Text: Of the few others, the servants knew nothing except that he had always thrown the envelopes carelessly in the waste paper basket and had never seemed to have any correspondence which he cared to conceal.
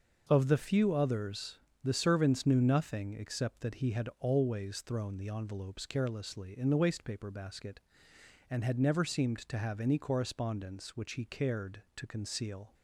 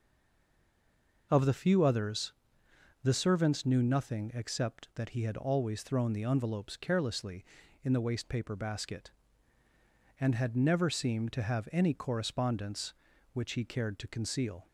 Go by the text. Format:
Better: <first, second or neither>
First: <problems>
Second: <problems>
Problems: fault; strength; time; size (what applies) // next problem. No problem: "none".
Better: first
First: none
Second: stays silent before the first word; noticeable; until 1.3 s; 1.3 s long